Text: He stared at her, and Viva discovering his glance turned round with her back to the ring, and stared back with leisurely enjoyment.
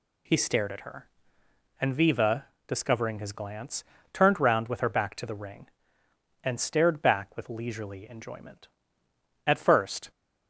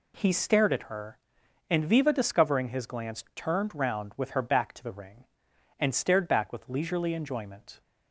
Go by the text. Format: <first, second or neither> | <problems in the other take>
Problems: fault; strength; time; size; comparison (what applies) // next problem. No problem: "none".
second | pauses between "Viva" and "discovering"; slight; at 2.4 s; 0.20 s long // pauses between "glance" and "turned"; slight; at 3.8 s; 0.28 s long // goes on to say "At first"; noticeable; from 9.4 s on; 0.64 s long